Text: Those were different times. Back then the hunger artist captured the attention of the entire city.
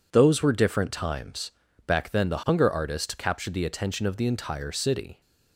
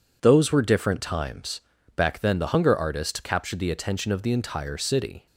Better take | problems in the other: neither | none

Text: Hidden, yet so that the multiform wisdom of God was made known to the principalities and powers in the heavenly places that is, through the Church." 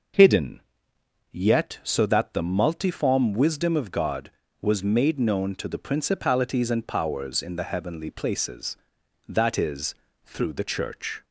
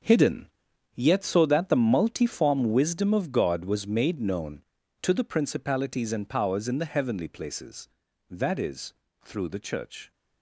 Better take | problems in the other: first | gets quieter; strong; throughout; 12.5 dB

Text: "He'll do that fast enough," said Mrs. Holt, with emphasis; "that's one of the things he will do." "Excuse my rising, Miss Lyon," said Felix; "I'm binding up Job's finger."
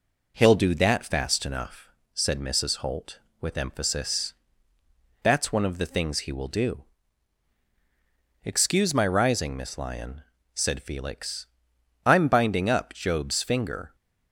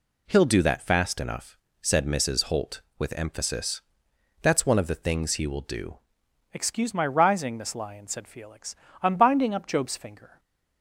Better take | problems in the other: first | changes voice at "Excuse"; from 6.5 s on; 3.8 s long

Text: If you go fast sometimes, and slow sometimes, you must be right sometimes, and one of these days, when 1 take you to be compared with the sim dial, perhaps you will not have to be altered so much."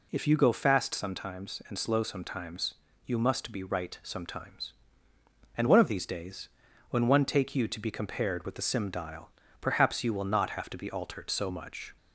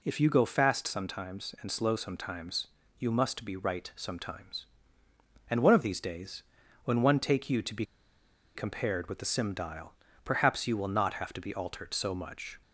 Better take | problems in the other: first | pauses between "be" and "compared"; noticeable; at 7.8 s; 0.69 s long

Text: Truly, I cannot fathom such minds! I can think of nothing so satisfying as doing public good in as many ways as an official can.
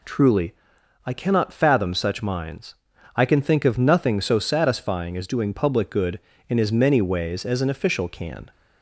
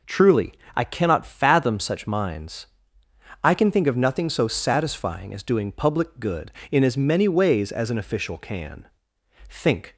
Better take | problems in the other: first | goes on to say "Think"; slight; from 9.4 s on; 0.46 s long

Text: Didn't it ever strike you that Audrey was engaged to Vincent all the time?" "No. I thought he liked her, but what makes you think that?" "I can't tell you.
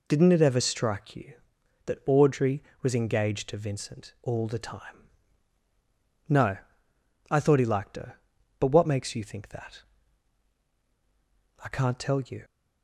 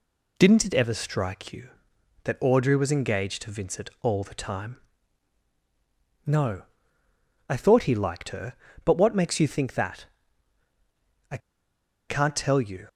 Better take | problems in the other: first | pauses between "I" and "can't"; noticeable; at 11.3 s; 0.70 s long

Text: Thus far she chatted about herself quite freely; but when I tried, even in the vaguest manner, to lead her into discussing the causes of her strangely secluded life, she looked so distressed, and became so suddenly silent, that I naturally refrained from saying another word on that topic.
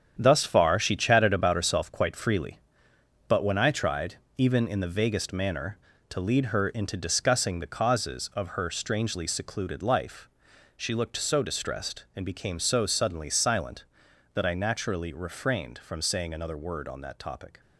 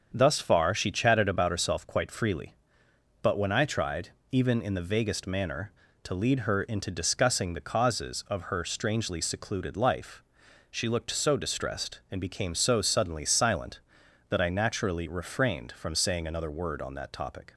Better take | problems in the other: second | gets quieter; strong; throughout; 9 dB // starts louder than the rest; strong; until 1.2 s; 8.5 dB; also in the second

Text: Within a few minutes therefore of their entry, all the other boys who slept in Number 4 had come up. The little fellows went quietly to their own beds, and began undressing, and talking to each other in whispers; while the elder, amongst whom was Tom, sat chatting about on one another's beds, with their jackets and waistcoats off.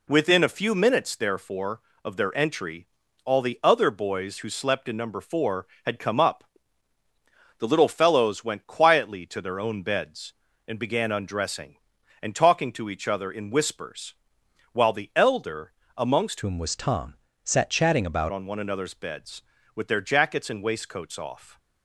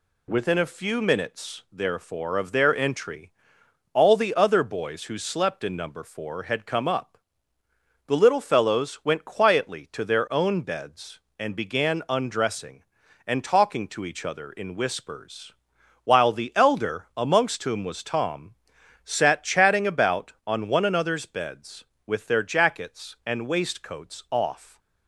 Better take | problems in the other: second | changes voice from "whom" to "about"; from 16.4 to 18.3 s; 1.9 s long

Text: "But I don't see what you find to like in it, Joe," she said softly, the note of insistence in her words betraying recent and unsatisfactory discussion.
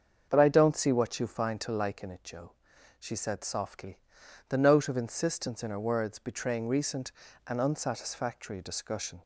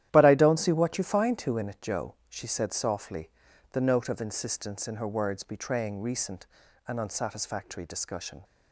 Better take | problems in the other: first | starts louder than the rest; strong; until 1.1 s; 12 dB; also in the first // skips "like"; at 1.5 s

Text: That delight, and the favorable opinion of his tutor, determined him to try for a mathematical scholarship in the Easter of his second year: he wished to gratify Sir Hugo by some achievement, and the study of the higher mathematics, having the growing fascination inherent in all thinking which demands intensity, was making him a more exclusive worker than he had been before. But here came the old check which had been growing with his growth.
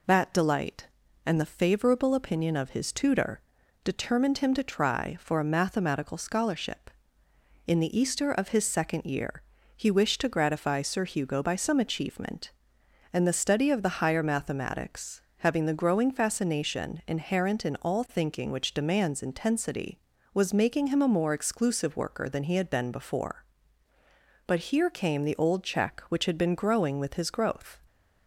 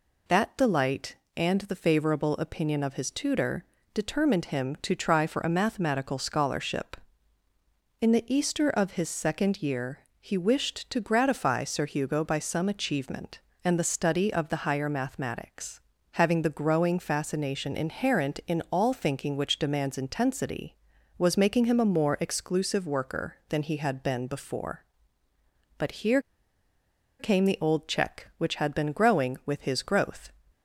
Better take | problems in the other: first | pauses between "here" and "came"; at 26.2 s; 0.99 s long

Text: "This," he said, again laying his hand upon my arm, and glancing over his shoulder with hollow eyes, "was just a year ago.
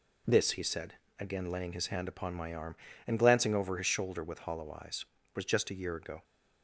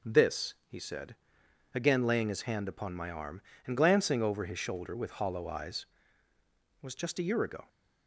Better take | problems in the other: neither | none

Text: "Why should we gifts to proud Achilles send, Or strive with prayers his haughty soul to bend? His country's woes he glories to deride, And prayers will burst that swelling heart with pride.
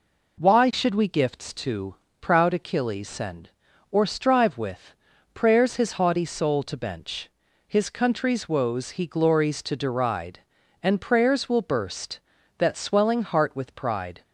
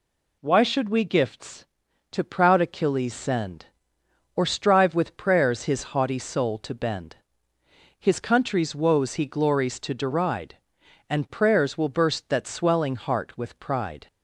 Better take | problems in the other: second | pauses between "to" and "proud"; slight; at 1.9 s; 0.26 s long // pauses between "with" and "prayers"; at 4.9 s; 0.40 s long // says "bench" for "bend"; at 6.7 s

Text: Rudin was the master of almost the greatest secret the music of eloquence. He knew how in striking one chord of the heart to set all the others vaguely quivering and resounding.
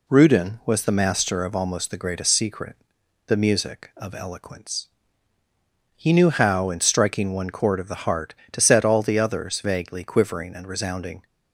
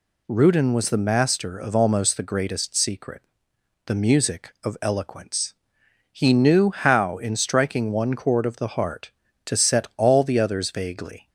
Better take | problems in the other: first | pauses between "secret" and "the"; noticeable; at 3.2 s; 0.66 s long; noticeable in the first // stops before "quivering and resounding"; at 11.2 s

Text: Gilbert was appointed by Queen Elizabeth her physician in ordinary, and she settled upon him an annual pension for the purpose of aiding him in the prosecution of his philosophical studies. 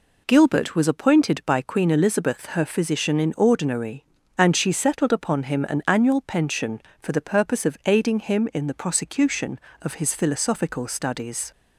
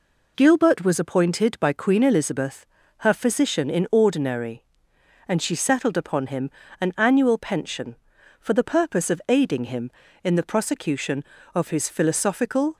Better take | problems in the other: first | pauses between "Elizabeth" and "her"; slight; at 2.6 s; 0.34 s long // pauses between "him" and "an"; slight; at 6.4 s; 0.30 s long // stops before "studies"; at 12.7 s

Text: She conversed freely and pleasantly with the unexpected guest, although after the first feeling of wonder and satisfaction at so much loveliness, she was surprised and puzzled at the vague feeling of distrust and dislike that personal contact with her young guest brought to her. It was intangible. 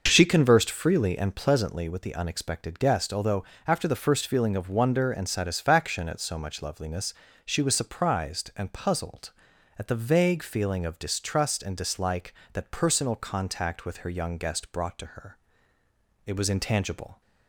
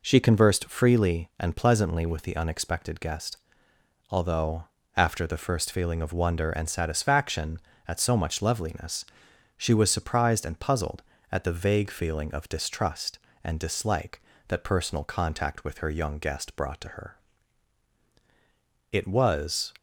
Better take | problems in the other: first | pauses between "although" and "after"; slight; at 4.6 s; 0.32 s long; slight in the first // stops before "intangible"; at 19.7 s

